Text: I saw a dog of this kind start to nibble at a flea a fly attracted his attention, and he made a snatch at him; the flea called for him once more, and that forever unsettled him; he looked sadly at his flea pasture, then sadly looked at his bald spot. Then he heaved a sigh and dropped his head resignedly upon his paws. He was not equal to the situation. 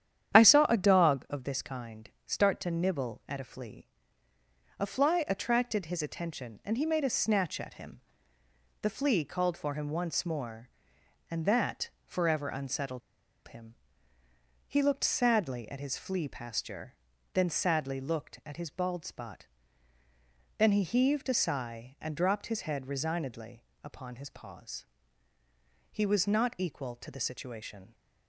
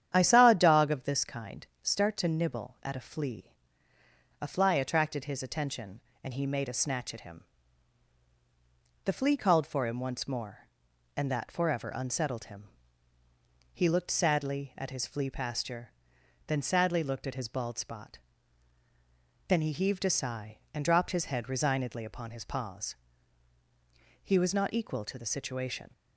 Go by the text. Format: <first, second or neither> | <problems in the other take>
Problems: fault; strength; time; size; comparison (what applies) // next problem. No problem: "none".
second | starts louder than the rest; strong; until 1.4 s; 9.5 dB; strong in the second // pauses between "kind" and "start"; slight; at 2.0 s; 0.16 s long; slight in the second // pauses between "flea" and "a"; noticeable; at 3.8 s; 0.92 s long; noticeable in the second // pauses between "that" and "forever"; slight; at 11.9 s; 0.16 s long // pauses between "unsettled" and "him"; noticeable; at 13.0 s; 0.47 s long // pauses between "resignedly" and "upon"; slight; at 23.6 s; 0.18 s long